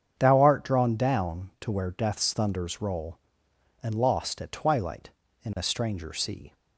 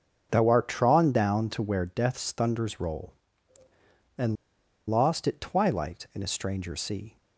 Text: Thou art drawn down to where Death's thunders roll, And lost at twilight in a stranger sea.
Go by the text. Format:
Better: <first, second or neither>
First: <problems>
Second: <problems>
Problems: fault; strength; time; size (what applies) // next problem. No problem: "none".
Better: first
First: starts louder than the rest; strong; until 1.1 s; 7.5 dB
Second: starts louder than the rest; until 1.3 s; 6.5 dB // pauses between "And" and "lost"; noticeable; at 4.3 s; 0.54 s long